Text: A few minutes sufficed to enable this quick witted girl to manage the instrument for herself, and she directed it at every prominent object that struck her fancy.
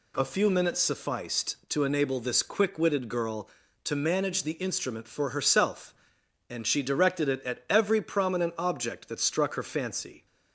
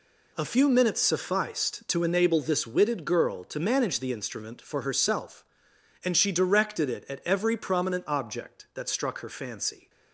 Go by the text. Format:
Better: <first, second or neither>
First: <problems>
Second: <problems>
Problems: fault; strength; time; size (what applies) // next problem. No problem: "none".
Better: first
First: none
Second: skips "quick"; at 2.6 s